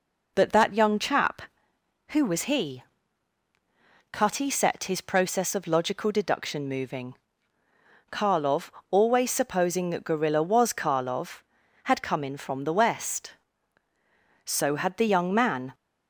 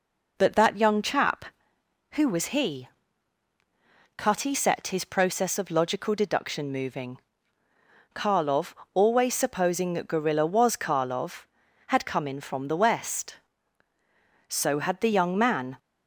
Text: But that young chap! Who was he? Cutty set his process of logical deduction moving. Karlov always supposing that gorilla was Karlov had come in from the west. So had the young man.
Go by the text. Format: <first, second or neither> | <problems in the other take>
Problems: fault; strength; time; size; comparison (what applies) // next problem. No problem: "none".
neither | pauses between "Karlov" and "always"; slight; the same in both